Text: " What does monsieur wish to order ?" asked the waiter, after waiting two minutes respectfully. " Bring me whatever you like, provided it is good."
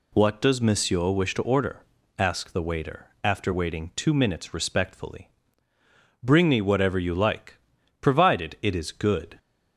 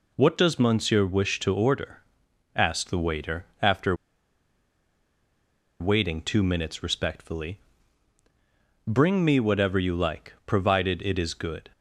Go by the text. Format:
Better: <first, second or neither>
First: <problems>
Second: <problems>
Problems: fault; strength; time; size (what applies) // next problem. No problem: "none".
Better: first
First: none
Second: pauses between "after" and "waiting"; strong; at 3.9 s; 1.8 s long